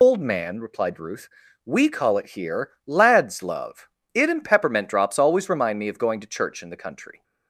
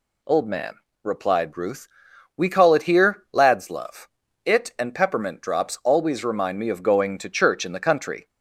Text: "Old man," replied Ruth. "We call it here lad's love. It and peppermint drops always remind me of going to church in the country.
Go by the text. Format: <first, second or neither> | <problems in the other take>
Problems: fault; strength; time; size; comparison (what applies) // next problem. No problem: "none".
second | loses the start of "Old"; at 0.0 s; 80 ms